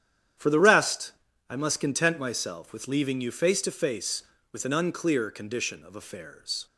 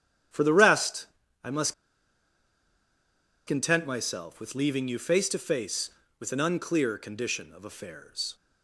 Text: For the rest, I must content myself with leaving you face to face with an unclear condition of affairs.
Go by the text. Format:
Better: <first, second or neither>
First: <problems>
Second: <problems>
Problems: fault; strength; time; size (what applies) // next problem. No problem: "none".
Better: first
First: starts louder than the rest; strong; until 1.7 s; 10 dB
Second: starts louder than the rest; strong; until 1.6 s; 10 dB // pauses between "must" and "content"; strong; at 1.7 s; 1.7 s long